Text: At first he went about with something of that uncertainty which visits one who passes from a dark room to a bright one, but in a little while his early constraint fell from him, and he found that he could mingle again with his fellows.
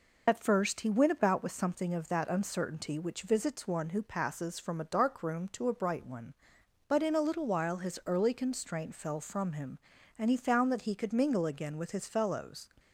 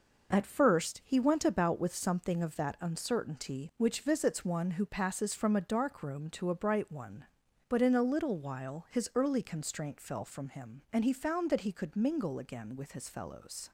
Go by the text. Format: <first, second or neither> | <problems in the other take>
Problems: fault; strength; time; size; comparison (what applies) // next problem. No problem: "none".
second | loses the start of "At"; at 0.2 s; 55 ms